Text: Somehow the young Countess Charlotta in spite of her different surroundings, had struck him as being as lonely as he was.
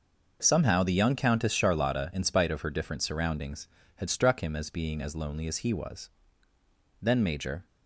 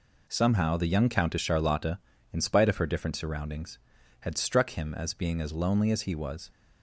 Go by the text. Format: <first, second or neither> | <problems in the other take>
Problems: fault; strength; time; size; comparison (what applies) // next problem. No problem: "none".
second | goes on to say "Then Major"; noticeable; from 7.0 s on; 0.64 s long